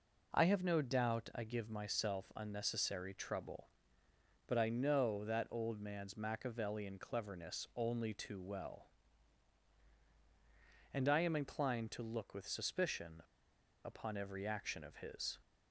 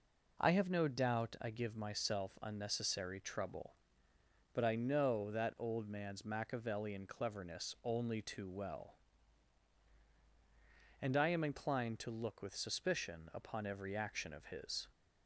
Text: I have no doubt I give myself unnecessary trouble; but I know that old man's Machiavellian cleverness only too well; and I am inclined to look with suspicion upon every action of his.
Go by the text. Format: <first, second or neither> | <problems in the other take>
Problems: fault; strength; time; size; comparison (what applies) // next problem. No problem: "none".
second | pauses between "suspicion" and "upon"; noticeable; at 13.2 s; 0.62 s long